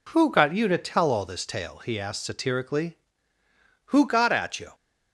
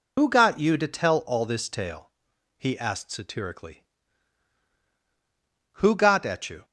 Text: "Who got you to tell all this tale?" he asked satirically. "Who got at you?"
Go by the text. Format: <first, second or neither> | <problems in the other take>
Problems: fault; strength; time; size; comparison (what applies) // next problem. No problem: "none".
first | loses the start of "Who"; at 0.1 s; 75 ms